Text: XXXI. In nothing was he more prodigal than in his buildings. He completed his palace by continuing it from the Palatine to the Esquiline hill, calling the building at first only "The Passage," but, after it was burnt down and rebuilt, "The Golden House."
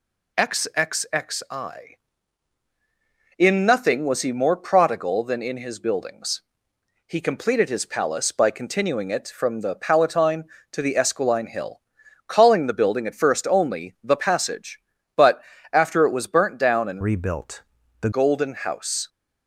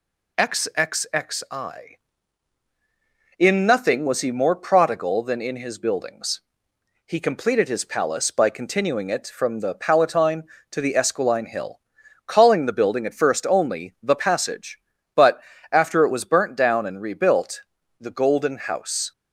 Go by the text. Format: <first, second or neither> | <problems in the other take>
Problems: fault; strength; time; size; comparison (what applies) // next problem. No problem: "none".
second | changes voice from "rebuilt" to "The"; from 17.0 to 18.0 s; 1.0 s long